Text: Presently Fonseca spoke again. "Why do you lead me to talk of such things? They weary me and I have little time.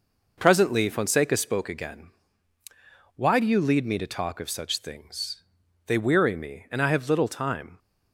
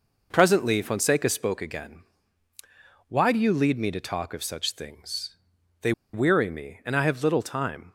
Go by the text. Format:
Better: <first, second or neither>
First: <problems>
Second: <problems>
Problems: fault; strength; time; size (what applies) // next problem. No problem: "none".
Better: first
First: none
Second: pauses between "They" and "weary"; slight; at 5.9 s; 0.22 s long